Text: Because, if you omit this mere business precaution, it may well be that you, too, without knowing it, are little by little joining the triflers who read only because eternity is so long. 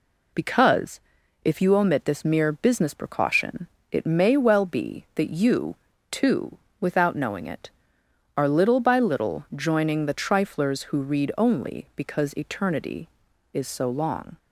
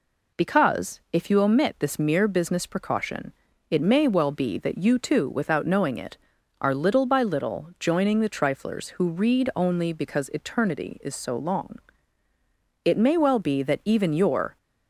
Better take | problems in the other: first | goes on to say "It may well be that even your"; strong; from 12.8 s on; 1.7 s long

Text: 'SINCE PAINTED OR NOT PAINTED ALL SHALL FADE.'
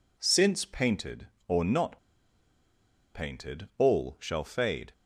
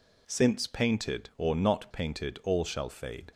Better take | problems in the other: second | pauses between "NOT" and "PAINTED"; at 1.9 s; 1.1 s long

